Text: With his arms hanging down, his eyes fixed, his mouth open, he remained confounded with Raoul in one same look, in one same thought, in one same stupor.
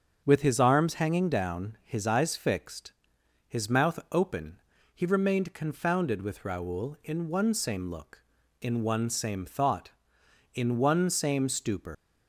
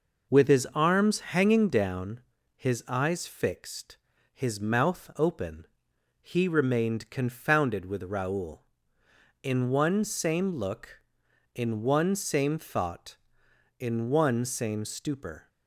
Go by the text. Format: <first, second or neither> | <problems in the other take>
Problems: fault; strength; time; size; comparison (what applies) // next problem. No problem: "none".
second | starts louder than the rest; until 1.2 s; 6.5 dB // leaves "stupor" unfinished; at 11.9 s; 120 ms